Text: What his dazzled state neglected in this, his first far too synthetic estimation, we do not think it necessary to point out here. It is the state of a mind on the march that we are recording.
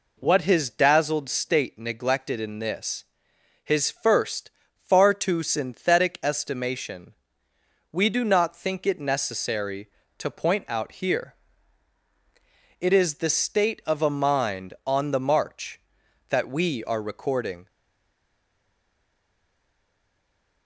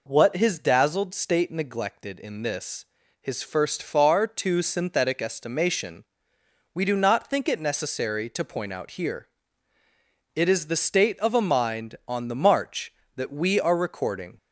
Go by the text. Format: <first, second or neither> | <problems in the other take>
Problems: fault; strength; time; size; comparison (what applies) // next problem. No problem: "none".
second | pauses between "first" and "far"; slight; at 4.4 s; 0.26 s long // stays silent after the last word; strong; from 17.6 s on; 3.0 s long